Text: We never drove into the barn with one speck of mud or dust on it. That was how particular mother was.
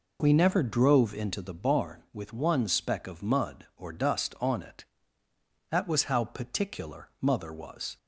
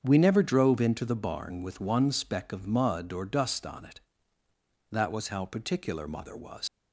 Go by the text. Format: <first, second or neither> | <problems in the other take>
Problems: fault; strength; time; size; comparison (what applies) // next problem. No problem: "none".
first | starts louder than the rest; strong; until 1.0 s; 7.5 dB // leaves "was" unfinished; at 6.6 s; 115 ms